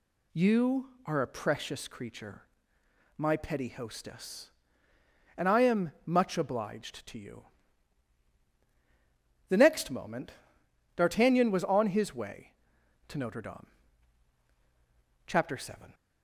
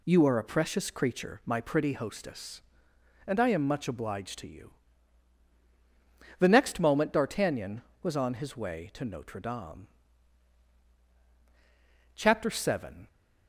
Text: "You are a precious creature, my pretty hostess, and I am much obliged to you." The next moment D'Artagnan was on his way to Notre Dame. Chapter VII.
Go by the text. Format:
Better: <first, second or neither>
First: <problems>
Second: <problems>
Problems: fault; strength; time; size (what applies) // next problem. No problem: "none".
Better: second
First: says "petty" for "pretty"; at 3.3 s // pauses between "moment" and "D'Artagnan"; noticeable; at 10.3 s; 0.62 s long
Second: none